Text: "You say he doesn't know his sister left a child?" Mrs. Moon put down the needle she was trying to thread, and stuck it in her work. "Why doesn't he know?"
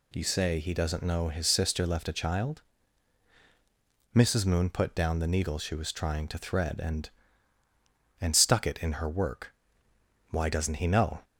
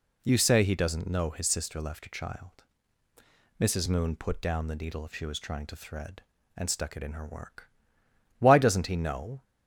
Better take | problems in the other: second | says "and" twice; at 8.1 s

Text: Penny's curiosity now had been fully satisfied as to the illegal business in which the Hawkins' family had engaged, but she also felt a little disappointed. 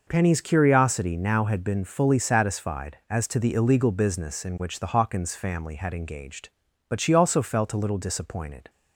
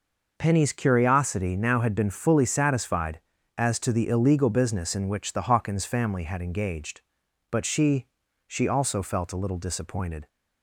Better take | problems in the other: first | says "she" twice; at 8.4 s

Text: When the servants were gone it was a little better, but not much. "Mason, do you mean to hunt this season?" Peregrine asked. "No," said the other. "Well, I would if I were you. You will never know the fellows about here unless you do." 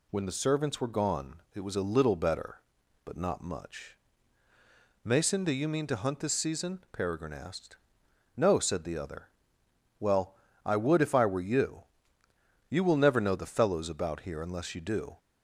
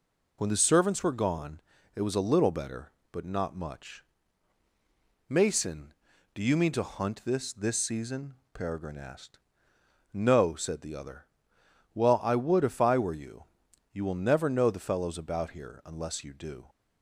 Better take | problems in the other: first | pauses between "gone" and "it"; slight; at 1.5 s; 0.36 s long // says "this" twice; at 7.5 s

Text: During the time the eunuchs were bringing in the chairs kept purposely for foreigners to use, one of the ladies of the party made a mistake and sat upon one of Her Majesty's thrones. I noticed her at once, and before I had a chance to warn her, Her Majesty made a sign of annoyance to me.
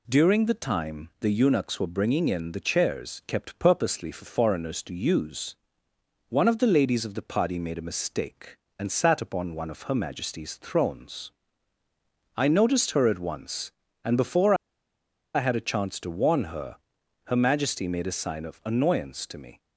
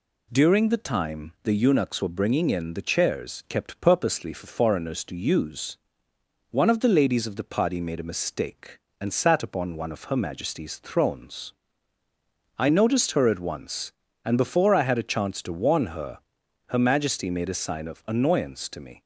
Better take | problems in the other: second | pauses between "before" and "I"; noticeable; at 14.5 s; 0.80 s long

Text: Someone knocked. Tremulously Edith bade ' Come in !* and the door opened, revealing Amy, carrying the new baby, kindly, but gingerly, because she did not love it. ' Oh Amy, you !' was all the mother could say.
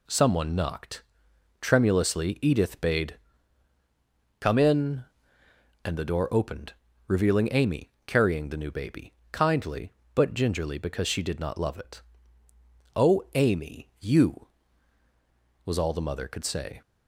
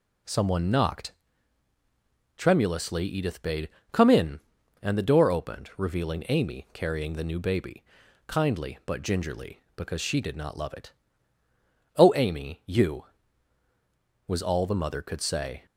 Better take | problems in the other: neither | none

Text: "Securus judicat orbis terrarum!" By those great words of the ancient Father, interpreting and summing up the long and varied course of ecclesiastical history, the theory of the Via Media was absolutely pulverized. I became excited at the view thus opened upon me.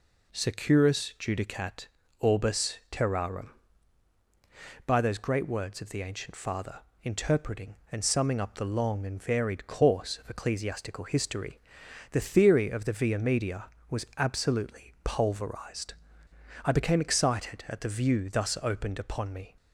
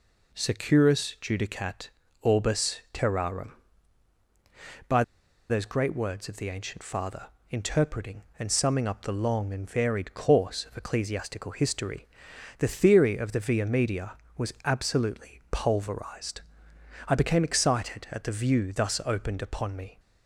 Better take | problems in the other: first | pauses between "judicat" and "orbis"; slight; at 1.8 s; 0.32 s long; slight in the first // pauses between "By" and "those"; noticeable; at 5.0 s; 0.47 s long

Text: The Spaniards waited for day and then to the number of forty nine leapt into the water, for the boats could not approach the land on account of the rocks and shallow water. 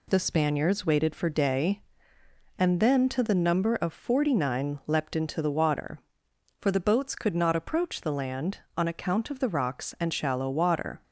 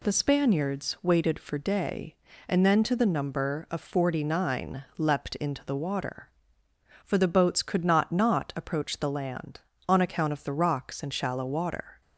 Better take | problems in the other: first | says "not" twice; at 8.1 s

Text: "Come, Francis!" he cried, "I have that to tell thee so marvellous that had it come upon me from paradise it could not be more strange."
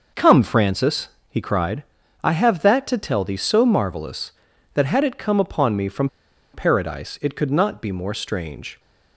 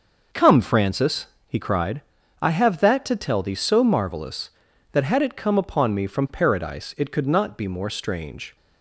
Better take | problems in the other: second | pauses between "from" and "paradise"; noticeable; at 6.0 s; 0.46 s long

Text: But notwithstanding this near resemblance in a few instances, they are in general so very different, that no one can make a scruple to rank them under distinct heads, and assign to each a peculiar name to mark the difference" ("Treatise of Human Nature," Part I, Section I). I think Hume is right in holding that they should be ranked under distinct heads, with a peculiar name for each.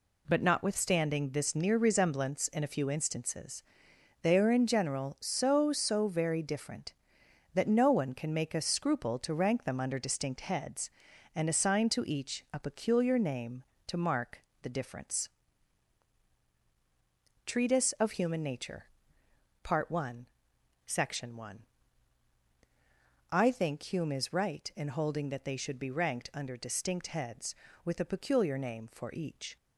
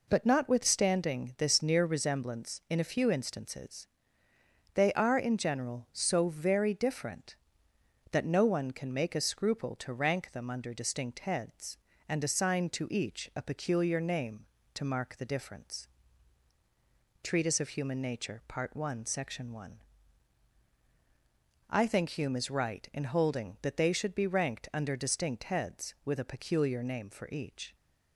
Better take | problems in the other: second | says "so" twice; at 5.7 s // pauses between "mark" and "the"; slight; at 14.4 s; 0.20 s long

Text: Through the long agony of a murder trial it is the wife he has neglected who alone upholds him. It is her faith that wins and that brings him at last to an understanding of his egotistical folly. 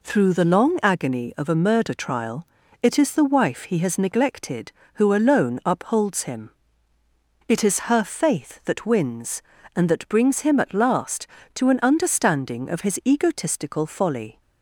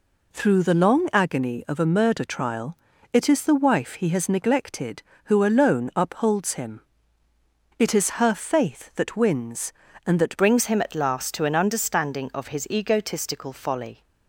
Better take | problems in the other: first | pauses between "trial" and "it"; slight; at 2.7 s; 0.36 s long; slight in the first // changes voice at "brings"; from 10.3 s on; 3.7 s long

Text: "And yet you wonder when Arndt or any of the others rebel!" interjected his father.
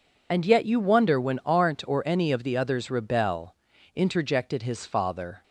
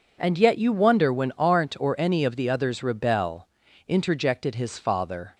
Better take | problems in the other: second | loses the start of "And"; at 0.3 s; 35 ms

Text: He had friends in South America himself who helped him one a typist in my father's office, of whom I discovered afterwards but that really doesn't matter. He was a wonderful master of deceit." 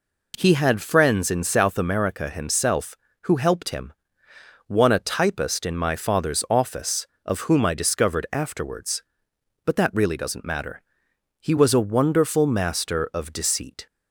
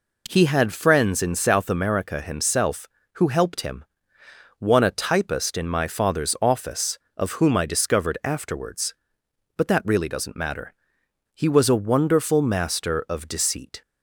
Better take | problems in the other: neither | pauses between "him" and "one"; noticeable; the same in both

